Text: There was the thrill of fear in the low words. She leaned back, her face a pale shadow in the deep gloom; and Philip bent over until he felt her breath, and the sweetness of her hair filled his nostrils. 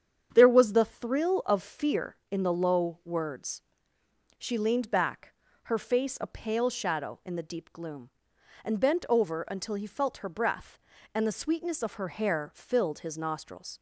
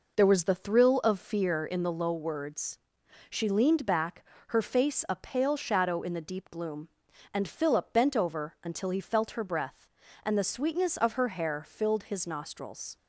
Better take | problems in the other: second | starts louder than the rest; strong; until 1.3 s; 8 dB // skips "Philip"; at 8.7 s

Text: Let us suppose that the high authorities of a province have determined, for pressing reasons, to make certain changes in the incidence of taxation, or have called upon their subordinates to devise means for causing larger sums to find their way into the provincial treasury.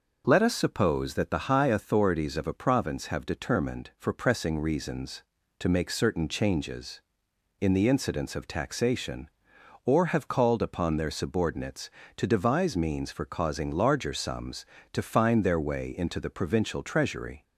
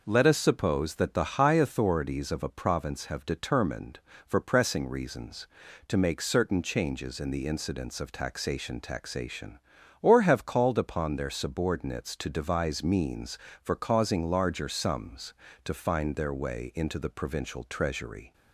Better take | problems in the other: first | says "taxation" twice; at 8.8 s

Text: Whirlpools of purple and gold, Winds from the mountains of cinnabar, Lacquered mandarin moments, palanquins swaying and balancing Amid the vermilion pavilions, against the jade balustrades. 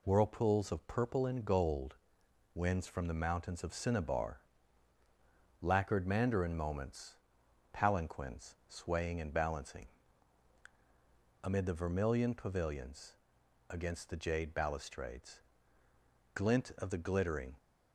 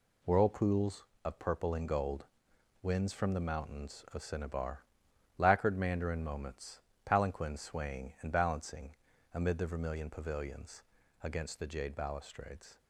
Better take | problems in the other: second | pauses between "balancing" and "Amid"; strong; at 9.8 s; 1.5 s long; also in the second // goes on to say "Glint of the glittering"; noticeable; from 16.3 s on; 1.2 s long

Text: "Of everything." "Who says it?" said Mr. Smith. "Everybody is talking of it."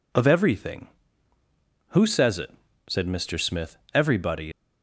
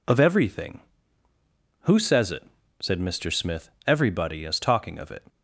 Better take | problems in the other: second | stops before "is talking of it"; at 4.5 s

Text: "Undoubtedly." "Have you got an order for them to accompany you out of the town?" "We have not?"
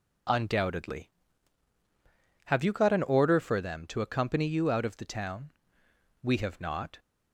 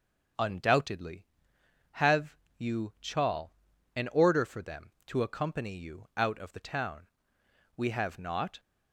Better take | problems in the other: first | pauses between "Have" and "you"; slight; at 2.3 s; 0.22 s long // says "chal" for "got"; at 2.9 s

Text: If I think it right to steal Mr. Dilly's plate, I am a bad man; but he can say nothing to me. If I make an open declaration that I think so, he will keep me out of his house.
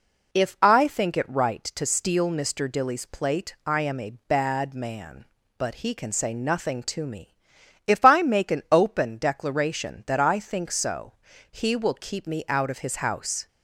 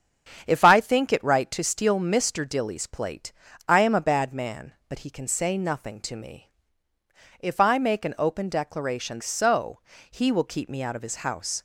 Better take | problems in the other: first | starts louder than the rest; strong; until 1.4 s; 8 dB // skips "that I think"; at 9.2 s

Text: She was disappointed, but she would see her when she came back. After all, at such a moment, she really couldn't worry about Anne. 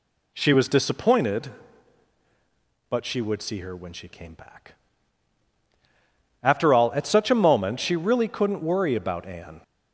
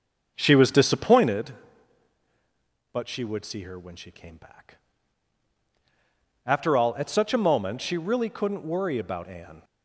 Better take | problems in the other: first | starts louder than the rest; until 1.4 s; 6 dB

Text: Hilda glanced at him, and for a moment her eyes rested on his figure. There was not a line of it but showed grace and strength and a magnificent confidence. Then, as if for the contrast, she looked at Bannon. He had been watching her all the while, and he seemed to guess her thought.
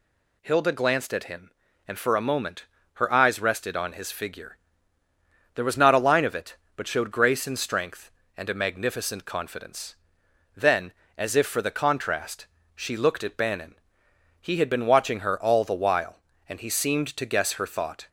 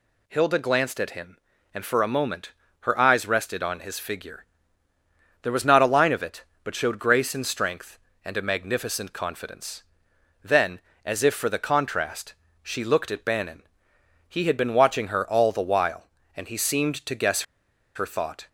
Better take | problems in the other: first | pauses between "moment" and "her"; slight; at 2.5 s; 0.28 s long; slight in the first // pauses between "guess" and "her"; noticeable; at 17.4 s; 0.51 s long

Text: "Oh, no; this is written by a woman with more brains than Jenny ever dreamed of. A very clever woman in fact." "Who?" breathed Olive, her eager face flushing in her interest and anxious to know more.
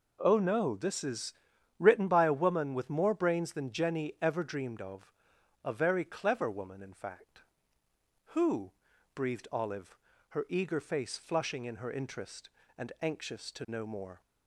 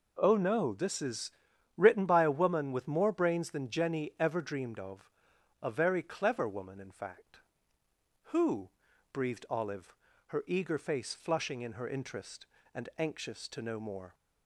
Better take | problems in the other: neither | pauses between "is" and "written"; noticeable; the same in both

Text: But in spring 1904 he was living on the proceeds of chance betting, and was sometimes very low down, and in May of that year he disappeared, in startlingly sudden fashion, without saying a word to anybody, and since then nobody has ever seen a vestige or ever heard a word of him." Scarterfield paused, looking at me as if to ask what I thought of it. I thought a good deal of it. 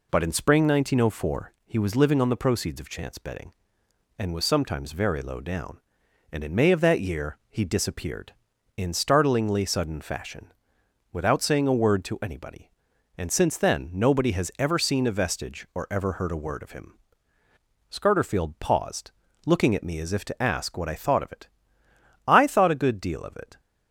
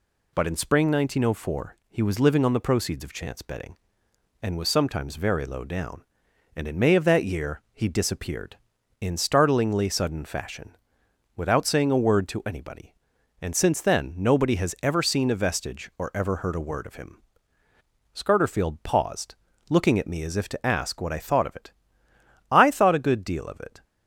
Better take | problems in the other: second | starts louder than the rest; slight; until 1.6 s; 3 dB

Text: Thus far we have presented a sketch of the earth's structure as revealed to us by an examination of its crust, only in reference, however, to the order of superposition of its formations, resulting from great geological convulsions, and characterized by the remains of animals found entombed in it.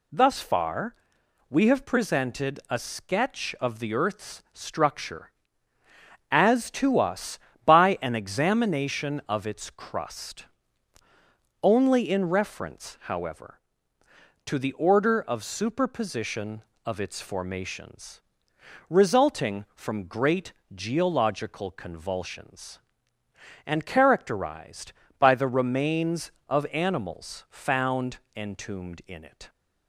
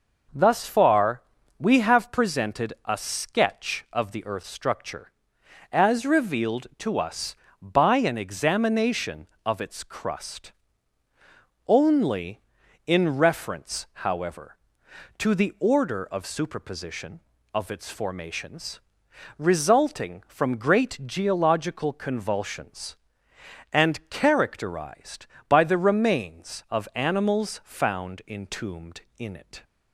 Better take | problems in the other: second | pauses between "far" and "we"; noticeable; at 0.9 s; 0.56 s long; slight in the second // skips "revealed"; at 6.6 s // pauses between "great" and "geological"; slight; at 20.5 s; 0.24 s long // pauses between "found" and "entombed"; slight; at 28.1 s; 0.18 s long

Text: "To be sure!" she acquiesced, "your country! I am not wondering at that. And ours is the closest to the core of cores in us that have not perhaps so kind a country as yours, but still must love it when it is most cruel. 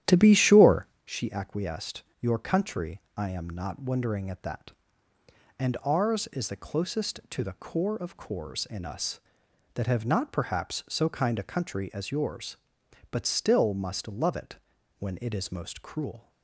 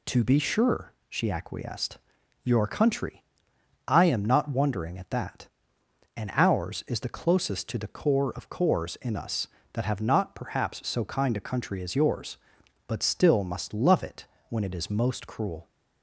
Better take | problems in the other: second | starts louder than the rest; strong; until 1.2 s; 11 dB // pauses between "it" and "when"; at 14.5 s; 0.42 s long; slight in the second

